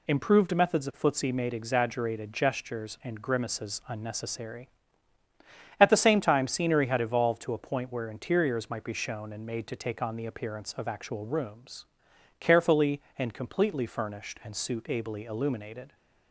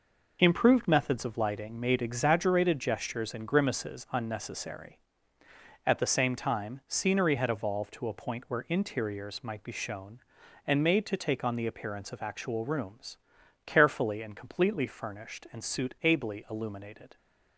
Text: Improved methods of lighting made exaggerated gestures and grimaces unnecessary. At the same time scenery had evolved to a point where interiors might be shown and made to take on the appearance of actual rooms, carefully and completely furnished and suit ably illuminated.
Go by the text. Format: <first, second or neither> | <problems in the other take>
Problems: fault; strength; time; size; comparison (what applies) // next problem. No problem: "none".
second | says "footsie" for "lighting"; at 1.0 s